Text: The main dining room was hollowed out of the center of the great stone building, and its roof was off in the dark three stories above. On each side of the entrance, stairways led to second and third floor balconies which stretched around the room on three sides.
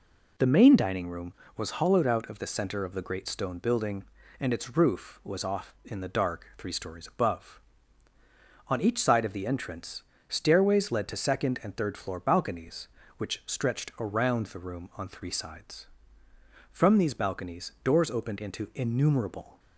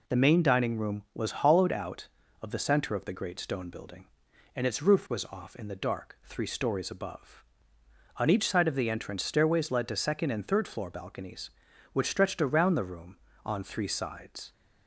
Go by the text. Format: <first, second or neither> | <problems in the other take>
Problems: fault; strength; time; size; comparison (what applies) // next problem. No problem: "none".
second | goes on to say "From these balconies doors opened into innumerable"; strong; from 16.7 s on; 2.8 s long